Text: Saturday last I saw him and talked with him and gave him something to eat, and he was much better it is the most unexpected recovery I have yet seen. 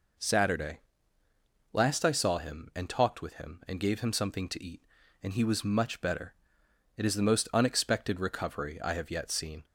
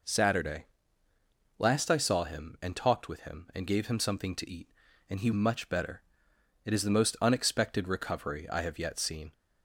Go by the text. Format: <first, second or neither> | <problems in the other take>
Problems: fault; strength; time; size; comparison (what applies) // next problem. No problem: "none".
first | pauses between "Saturday" and "last"; noticeable; at 0.6 s; 0.94 s long; noticeable in the first // skips "was"; at 5.3 s // pauses between "better" and "it"; noticeable; at 6.0 s; 0.62 s long; noticeable in the first